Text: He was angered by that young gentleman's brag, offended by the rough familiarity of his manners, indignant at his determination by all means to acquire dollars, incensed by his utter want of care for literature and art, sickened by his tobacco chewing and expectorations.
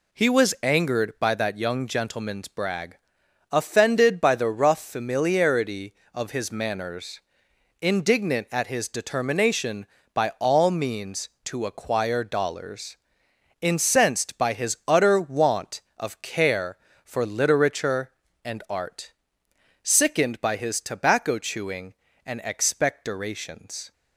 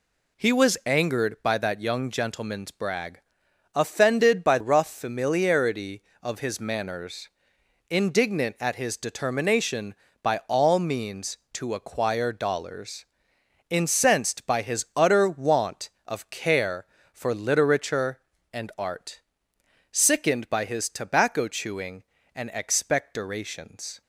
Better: first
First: none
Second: skips "the"; at 4.5 s

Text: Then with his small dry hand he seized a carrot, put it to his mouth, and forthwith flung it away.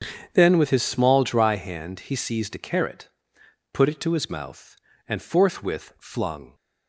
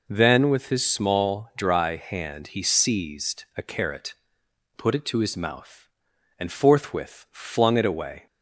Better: second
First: starts louder than the rest; strong; until 1.3 s; 7.5 dB // stops before "it away"; at 6.5 s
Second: none

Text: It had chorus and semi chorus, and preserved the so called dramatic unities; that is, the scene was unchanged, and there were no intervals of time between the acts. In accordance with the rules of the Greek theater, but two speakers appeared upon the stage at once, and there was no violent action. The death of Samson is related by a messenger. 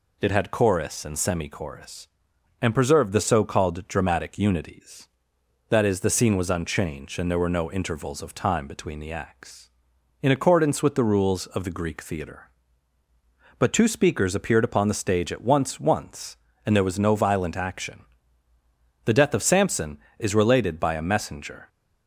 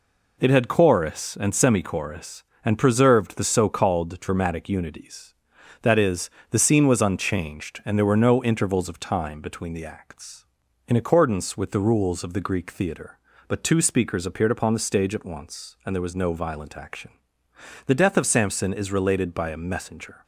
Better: second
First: says "once" twice; at 15.7 s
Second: none

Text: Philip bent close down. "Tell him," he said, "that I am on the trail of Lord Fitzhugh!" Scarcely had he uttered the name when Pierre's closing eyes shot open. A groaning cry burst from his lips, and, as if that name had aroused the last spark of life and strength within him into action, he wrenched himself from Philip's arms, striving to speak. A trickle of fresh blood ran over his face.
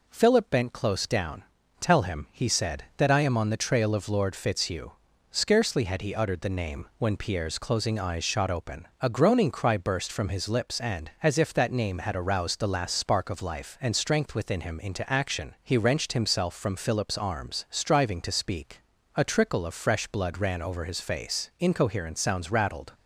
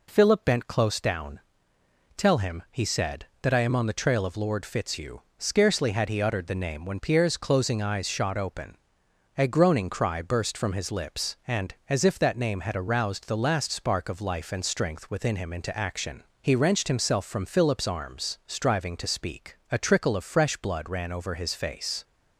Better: second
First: goes on to say "Incoherent sounds rattled"; from 21.5 s on; 1.3 s long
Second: none

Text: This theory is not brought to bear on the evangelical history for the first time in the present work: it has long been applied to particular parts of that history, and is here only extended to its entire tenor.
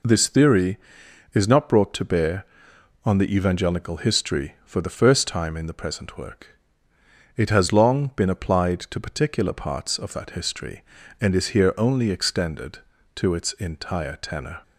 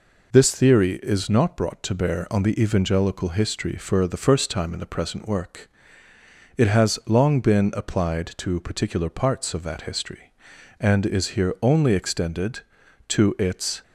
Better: first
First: none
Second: stops before "entire tenor"; at 13.8 s

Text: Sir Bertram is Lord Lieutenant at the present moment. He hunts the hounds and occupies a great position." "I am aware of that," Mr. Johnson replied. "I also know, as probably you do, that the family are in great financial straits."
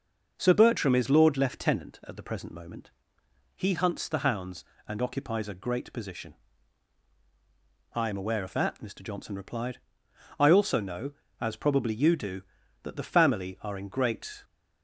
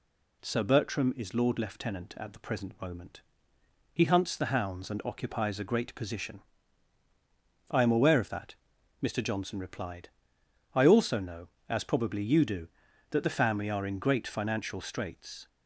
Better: second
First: stops before "financial straits"; at 14.4 s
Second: none

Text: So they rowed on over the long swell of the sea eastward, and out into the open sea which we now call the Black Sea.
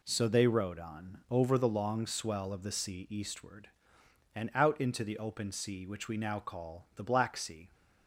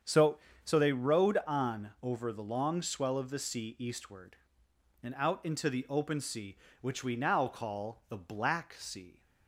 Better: first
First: none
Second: starts louder than the rest; strong; until 1.3 s; 7.5 dB // says "So" twice; at 0.6 s

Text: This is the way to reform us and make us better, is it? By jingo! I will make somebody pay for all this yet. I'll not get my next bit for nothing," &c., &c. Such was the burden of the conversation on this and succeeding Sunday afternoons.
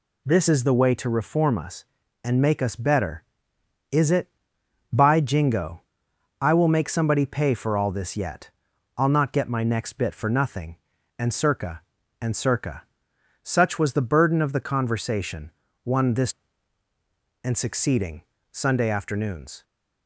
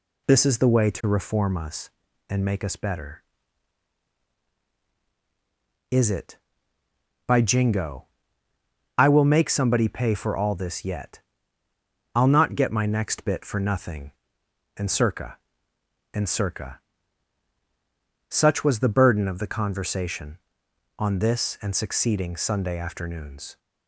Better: second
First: says "one" for "on"; at 15.8 s // pauses between "succeeding" and "Sunday"; slight; at 18.2 s; 0.28 s long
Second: none

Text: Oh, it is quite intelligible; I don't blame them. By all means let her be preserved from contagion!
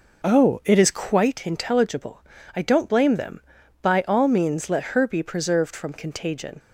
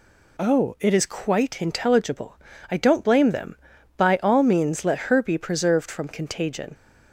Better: second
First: starts louder than the rest; noticeable; until 1.4 s; 5 dB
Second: none

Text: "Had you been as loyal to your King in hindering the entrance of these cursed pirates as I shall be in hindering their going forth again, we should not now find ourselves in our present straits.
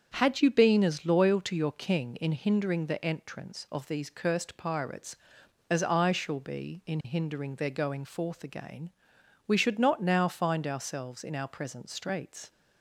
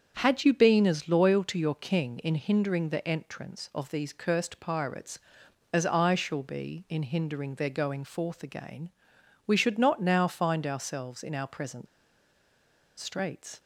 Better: first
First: starts louder than the rest; strong; until 1.1 s; 7.5 dB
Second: starts louder than the rest; strong; until 1.2 s; 7.5 dB // pauses between "present" and "straits"; at 11.8 s; 1.1 s long

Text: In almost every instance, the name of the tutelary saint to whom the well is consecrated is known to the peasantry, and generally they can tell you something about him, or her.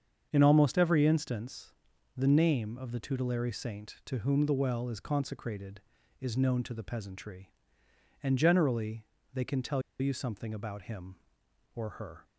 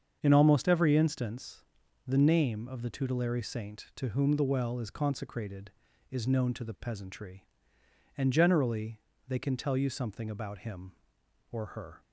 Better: second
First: starts louder than the rest; strong; until 1.3 s; 7 dB // pauses between "generally" and "they"; slight; at 9.0 s; 0.28 s long // pauses between "tell" and "you"; slight; at 9.8 s; 0.19 s long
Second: starts louder than the rest; strong; until 1.2 s; 7 dB // pauses between "generally" and "they"; slight; at 8.9 s; 0.28 s long

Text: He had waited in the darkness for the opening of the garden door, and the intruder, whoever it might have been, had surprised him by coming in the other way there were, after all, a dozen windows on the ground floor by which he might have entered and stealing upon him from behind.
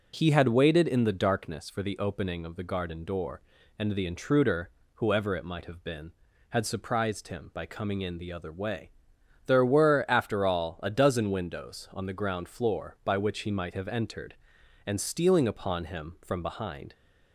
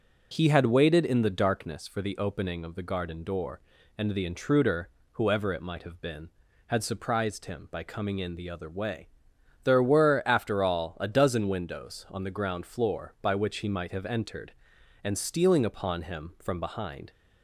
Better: neither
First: pauses between "way" and "there"; noticeable; at 8.9 s; 0.56 s long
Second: pauses between "way" and "there"; noticeable; at 9.0 s; 0.56 s long

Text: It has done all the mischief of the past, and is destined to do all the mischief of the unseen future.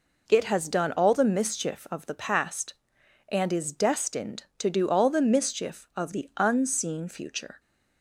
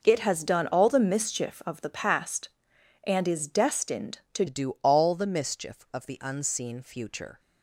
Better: first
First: none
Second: changes voice at "do"; from 4.4 s on; 2.9 s long

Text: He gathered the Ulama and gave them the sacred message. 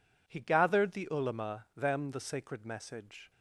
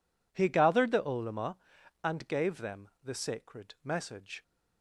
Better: second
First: skips "and gave"; at 1.7 s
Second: none

